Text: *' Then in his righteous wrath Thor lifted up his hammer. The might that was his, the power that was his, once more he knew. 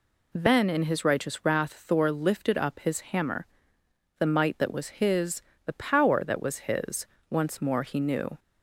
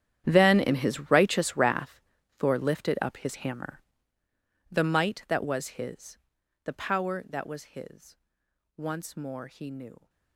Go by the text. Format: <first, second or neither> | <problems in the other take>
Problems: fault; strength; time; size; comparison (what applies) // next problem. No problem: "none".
first | gets quieter; strong; throughout; 17.5 dB // pauses between "wrath" and "Thor"; at 2.0 s; 0.38 s long